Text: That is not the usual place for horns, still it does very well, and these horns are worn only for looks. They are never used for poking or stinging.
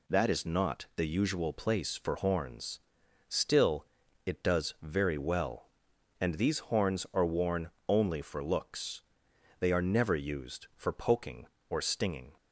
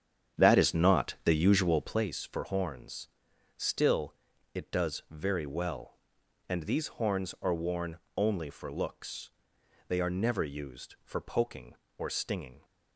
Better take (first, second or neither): first